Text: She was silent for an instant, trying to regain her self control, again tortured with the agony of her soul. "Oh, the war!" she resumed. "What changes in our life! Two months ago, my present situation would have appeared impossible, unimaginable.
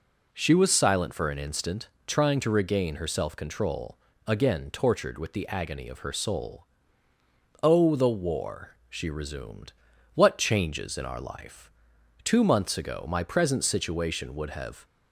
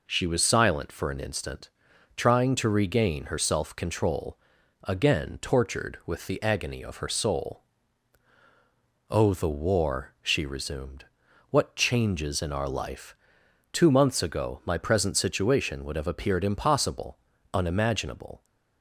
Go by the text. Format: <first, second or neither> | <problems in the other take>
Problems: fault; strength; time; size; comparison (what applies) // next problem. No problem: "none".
second | stops before "appeared impossible unimaginable"; at 14.8 s